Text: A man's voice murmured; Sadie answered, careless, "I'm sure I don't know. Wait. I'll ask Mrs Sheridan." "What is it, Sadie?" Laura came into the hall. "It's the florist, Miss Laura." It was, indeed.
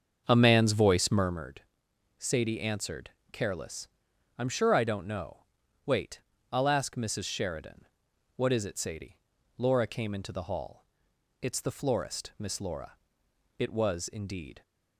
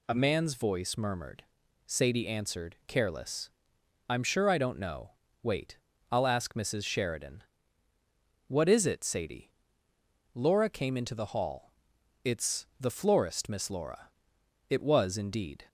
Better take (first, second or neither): second